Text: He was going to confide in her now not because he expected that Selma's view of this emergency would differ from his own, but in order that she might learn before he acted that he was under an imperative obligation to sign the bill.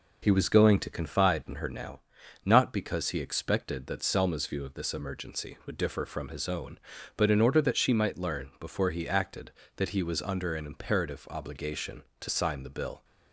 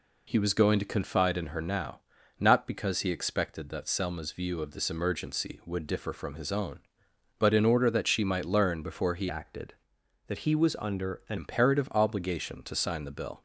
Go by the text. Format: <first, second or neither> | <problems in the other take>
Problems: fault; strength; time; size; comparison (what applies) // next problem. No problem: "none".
first | pauses between "now" and "not"; at 2.0 s; 0.38 s long; also in the first // changes voice from "acted" to "an"; from 9.2 to 11.3 s; 2.1 s long